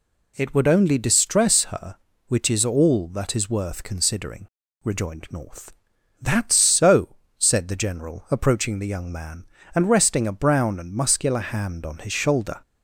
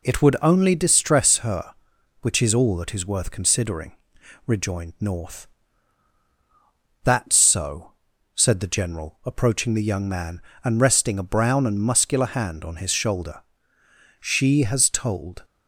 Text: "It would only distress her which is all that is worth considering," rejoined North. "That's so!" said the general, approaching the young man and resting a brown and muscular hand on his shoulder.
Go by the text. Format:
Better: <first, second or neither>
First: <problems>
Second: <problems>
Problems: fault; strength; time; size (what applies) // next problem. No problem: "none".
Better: first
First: none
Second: goes on to say "She has told"; noticeable; from 14.1 s on; 1.2 s long